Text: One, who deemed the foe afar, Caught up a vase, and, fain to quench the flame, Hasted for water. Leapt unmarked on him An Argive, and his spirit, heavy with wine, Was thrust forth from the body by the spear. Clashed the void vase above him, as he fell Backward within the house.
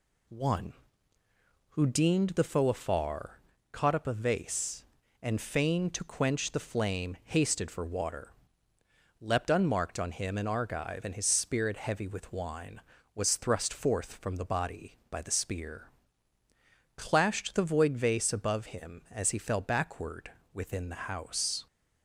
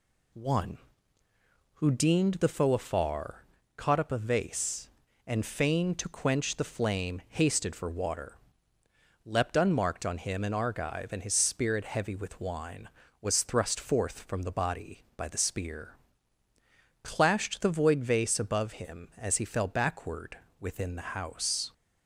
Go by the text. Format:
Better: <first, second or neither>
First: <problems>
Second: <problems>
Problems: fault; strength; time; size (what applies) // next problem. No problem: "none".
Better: neither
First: pauses between "Backward" and "within"; slight; at 20.3 s; 0.24 s long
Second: pauses between "Backward" and "within"; slight; at 20.3 s; 0.24 s long